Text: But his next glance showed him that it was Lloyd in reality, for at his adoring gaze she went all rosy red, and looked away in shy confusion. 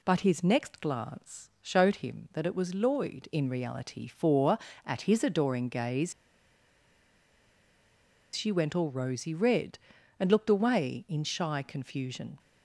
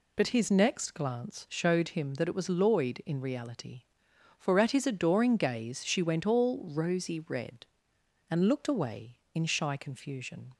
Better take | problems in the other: second | pauses between "gaze" and "she"; strong; at 6.1 s; 2.2 s long

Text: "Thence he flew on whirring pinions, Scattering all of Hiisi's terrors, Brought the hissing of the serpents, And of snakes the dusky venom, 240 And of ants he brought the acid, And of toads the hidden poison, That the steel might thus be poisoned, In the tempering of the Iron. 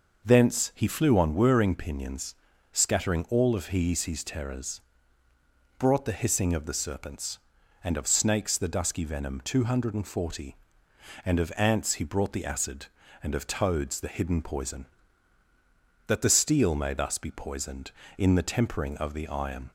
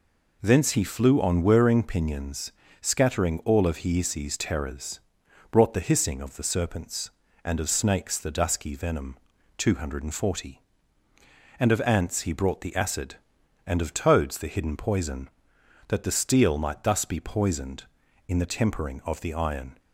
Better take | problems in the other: second | says "may" for "might"; at 16.7 s

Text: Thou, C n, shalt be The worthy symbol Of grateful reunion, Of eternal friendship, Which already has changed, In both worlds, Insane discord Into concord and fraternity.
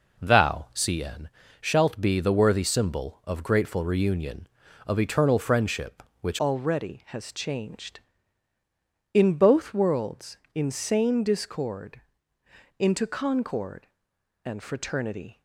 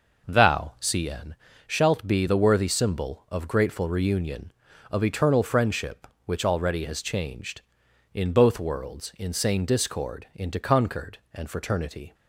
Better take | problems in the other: second | changes voice at "already"; from 6.3 s on; 9.1 s long // pauses between "discord" and "Into"; noticeable; at 12.0 s; 0.76 s long

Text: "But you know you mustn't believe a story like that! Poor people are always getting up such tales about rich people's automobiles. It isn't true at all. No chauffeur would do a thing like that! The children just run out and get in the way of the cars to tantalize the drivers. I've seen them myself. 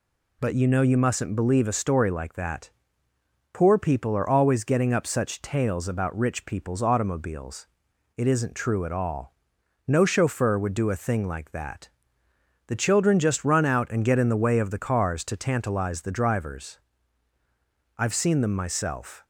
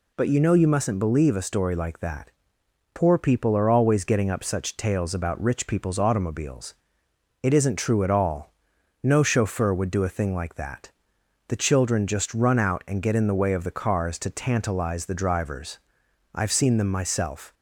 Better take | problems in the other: neither | none

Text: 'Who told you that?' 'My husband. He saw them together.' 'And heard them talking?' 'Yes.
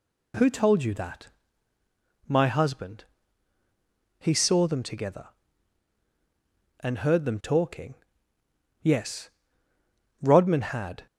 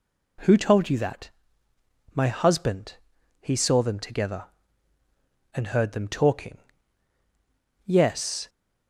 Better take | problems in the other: second | goes on to say "Rodman had"; noticeable; from 10.2 s on; 0.84 s long

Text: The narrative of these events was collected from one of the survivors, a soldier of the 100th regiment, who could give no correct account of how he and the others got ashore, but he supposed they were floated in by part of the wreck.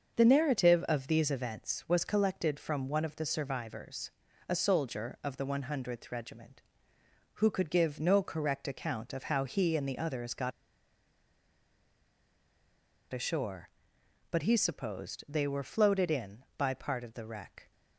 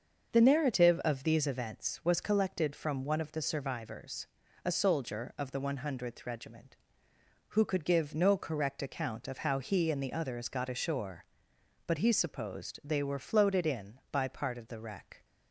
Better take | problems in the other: second | starts louder than the rest; until 1.2 s; 6.5 dB; also in the second // pauses between "got" and "ashore"; strong; at 10.5 s; 2.6 s long

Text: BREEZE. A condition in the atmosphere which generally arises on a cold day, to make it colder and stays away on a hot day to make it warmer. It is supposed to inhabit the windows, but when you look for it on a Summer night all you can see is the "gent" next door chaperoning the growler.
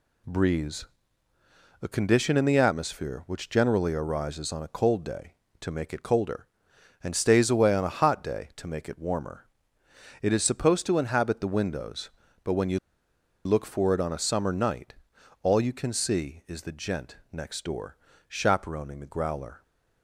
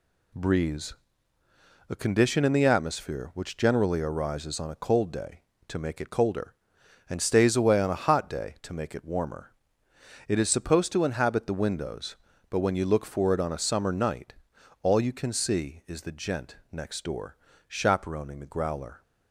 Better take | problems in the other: second | pauses between "you" and "look"; noticeable; at 12.7 s; 0.67 s long // pauses between "night" and "all"; noticeable; at 14.9 s; 0.48 s long; noticeable in the second // pauses between "gent" and "next"; slight; at 17.1 s; 0.16 s long; slight in the second // pauses between "door" and "chaperoning"; slight; at 17.9 s; 0.32 s long; slight in the second

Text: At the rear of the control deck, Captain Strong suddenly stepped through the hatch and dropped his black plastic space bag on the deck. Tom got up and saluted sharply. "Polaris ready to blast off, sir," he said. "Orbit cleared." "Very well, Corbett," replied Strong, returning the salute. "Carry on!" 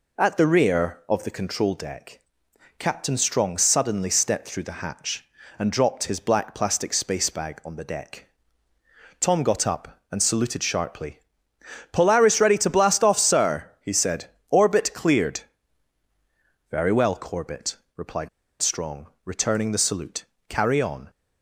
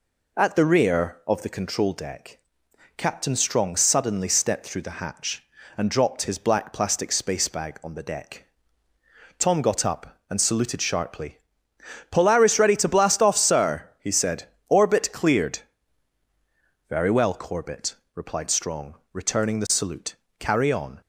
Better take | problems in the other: second | pauses between "replied" and "Strong"; slight; at 18.2 s; 0.32 s long

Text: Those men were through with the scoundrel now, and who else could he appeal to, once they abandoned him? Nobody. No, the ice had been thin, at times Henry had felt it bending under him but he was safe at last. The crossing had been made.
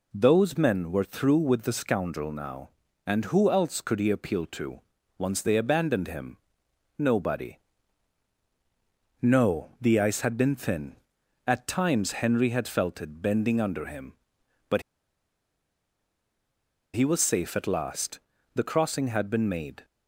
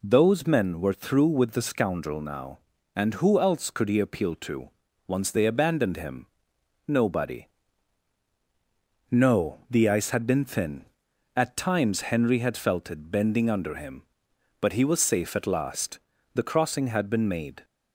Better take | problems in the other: second | pauses between "but" and "he"; strong; at 14.8 s; 2.1 s long

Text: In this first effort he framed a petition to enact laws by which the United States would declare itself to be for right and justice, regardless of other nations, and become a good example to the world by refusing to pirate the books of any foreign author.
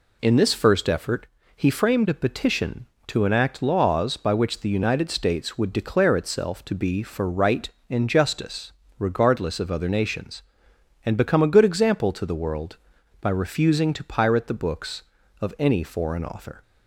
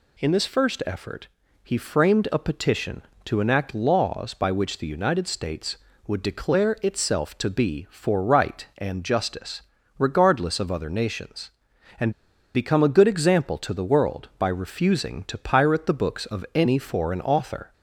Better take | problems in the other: first | pauses between "effort" and "he"; slight; at 1.2 s; 0.36 s long; slight in the first // pauses between "and" and "become"; at 12.1 s; 0.42 s long

